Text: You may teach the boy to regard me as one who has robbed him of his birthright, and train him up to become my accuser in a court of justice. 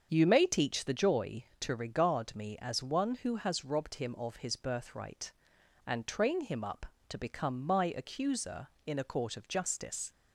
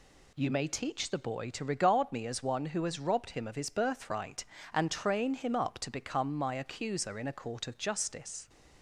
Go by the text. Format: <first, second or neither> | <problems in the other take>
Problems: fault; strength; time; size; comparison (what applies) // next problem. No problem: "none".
second | starts louder than the rest; strong; until 1.1 s; 7 dB // says "joy" for "boy"; at 0.9 s